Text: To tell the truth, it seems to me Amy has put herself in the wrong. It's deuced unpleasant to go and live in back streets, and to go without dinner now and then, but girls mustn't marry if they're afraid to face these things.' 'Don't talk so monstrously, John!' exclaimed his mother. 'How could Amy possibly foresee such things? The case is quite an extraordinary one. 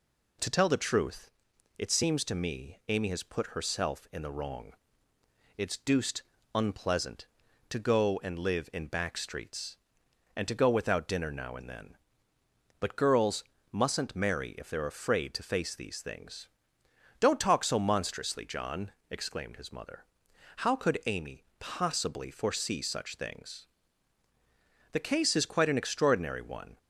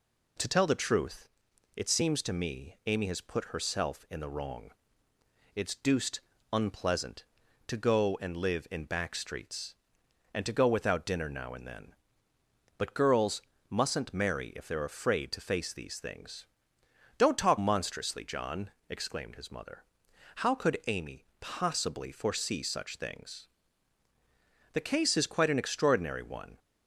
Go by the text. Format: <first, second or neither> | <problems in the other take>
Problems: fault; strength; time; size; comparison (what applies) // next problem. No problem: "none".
first | pauses between "deuced" and "unpleasant"; slight; at 6.1 s; 0.32 s long; slight in the first // pauses between "girls" and "mustn't"; slight; at 13.4 s; 0.28 s long; slight in the first // skips "so"; at 17.5 s // pauses between "Amy" and "possibly"; slight; at 21.2 s; 0.16 s long; slight in the first